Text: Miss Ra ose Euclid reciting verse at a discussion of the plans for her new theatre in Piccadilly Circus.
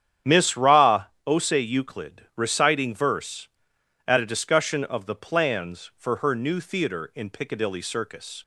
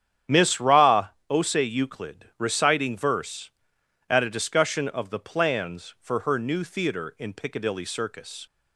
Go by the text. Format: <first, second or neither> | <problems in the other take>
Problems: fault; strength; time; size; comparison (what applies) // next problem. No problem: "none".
neither | starts louder than the rest; strong; the same in both // pauses between "Ra" and "ose"; slight; the same in both